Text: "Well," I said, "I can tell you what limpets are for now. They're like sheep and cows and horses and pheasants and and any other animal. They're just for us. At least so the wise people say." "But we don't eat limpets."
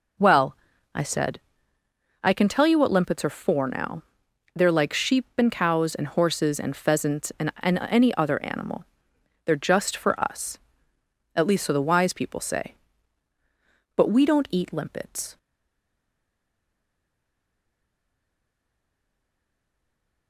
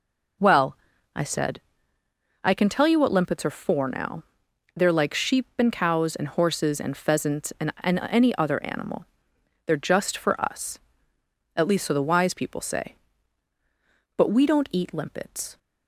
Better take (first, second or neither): second